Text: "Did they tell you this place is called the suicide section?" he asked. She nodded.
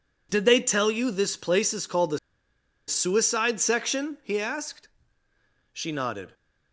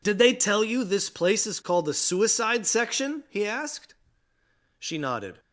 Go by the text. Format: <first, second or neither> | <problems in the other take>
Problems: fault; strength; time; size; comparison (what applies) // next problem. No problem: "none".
second | pauses between "the" and "suicide"; noticeable; at 2.1 s; 0.69 s long